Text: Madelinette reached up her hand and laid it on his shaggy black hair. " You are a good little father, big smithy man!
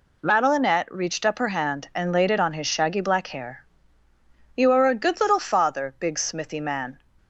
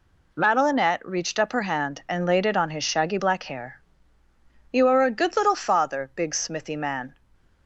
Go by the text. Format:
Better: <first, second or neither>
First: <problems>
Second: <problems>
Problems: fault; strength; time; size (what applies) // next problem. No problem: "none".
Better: neither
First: none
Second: none